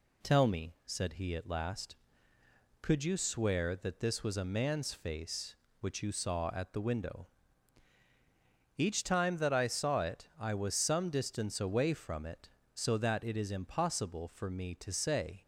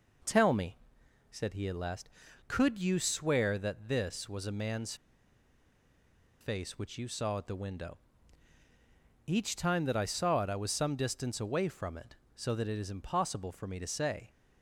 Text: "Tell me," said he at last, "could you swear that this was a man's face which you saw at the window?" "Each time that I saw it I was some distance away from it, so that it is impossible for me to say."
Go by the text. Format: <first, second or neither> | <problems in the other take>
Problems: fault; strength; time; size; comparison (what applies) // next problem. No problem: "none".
first | pauses between "man's" and "face"; strong; at 4.9 s; 1.4 s long